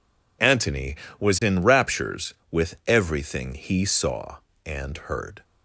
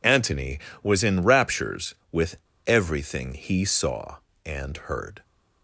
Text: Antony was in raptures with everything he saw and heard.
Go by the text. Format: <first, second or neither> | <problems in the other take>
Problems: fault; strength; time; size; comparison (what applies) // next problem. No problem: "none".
first | pauses between "with" and "everything"; slight; at 2.3 s; 0.31 s long